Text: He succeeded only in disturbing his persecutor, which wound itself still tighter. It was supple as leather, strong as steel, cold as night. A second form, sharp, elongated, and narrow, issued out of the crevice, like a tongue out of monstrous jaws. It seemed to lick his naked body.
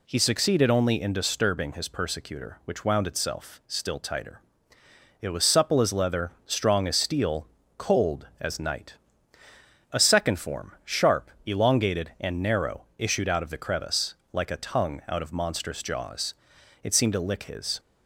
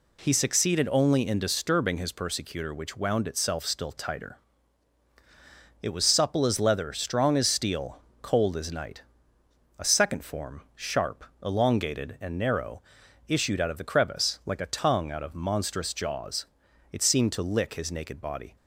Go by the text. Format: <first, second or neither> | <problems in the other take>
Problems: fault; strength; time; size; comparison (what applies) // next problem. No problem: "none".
second | stops before "naked body"; at 17.7 s